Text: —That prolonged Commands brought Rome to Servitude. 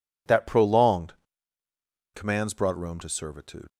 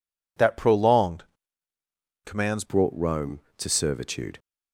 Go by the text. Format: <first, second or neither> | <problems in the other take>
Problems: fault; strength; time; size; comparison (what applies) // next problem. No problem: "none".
first | pauses between "prolonged" and "Commands"; at 1.2 s; 1.0 s long; also in the first // changes voice at "brought"; from 2.6 s on; 1.7 s long